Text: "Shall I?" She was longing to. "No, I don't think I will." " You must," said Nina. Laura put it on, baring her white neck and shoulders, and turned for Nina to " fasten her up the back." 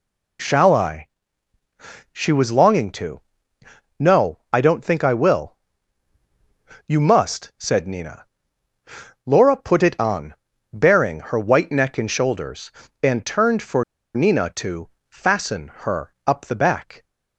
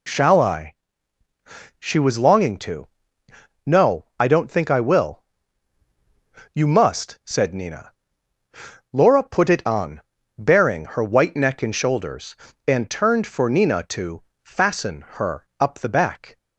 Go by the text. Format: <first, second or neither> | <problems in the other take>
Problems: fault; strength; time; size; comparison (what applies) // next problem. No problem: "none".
second | pauses between "for" and "Nina"; slight; at 13.8 s; 0.31 s long